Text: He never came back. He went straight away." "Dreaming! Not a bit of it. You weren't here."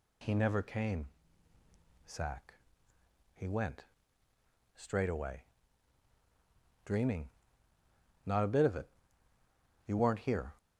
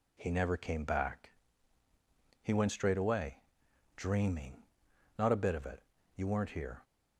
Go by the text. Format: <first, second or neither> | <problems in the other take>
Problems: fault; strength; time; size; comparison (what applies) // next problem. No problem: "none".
second | says "sack" for "back"; at 2.0 s // pauses between "went" and "straight"; noticeable; at 3.8 s; 0.90 s long